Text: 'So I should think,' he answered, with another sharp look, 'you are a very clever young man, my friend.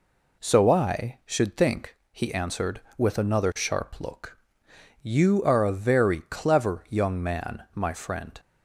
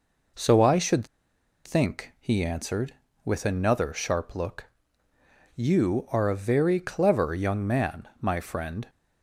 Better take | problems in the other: first | pauses between "should" and "think"; noticeable; at 1.0 s; 0.58 s long

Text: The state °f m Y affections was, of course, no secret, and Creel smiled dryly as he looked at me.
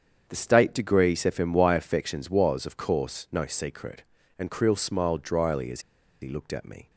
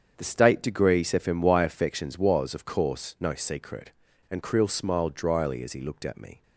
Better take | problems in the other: second | starts louder than the rest; strong; until 1.2 s; 7.5 dB; strong in the second // pauses between "as" and "he"; at 5.8 s; 0.41 s long

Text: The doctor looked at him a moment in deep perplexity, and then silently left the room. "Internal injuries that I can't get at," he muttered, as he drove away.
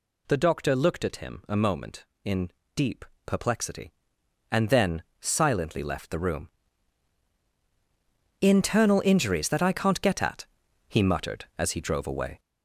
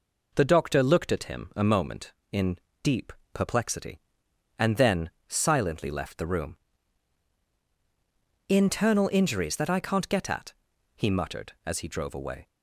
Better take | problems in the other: second | gets louder; noticeable; throughout; 5.5 dB // pauses between "in" and "deep"; slight; at 2.4 s; 0.26 s long; slight in the second // pauses between "deep" and "perplexity"; slight; at 3.0 s; 0.22 s long; slight in the second // pauses between "then" and "silently"; slight; at 5.0 s; 0.18 s long; slight in the second

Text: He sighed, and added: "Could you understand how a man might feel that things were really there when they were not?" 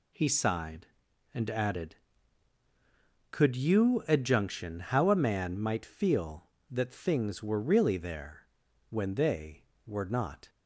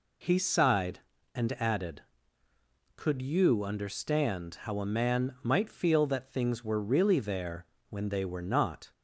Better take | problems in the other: second | says "adjunction" for "understand"; at 4.0 s // pauses between "there" and "when"; noticeable; at 8.4 s; 0.46 s long; slight in the second

